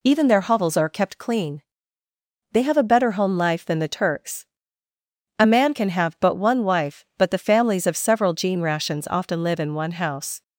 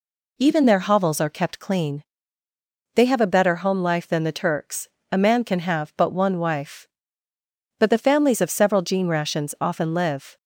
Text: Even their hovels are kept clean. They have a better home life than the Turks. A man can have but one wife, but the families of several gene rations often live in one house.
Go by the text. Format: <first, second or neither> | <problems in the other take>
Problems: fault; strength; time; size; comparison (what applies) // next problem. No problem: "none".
first | stops before "in one house"; at 10.3 s